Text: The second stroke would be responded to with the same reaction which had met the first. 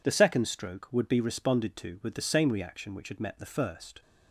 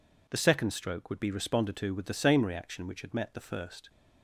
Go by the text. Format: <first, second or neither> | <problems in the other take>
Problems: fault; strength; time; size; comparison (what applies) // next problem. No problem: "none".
neither | none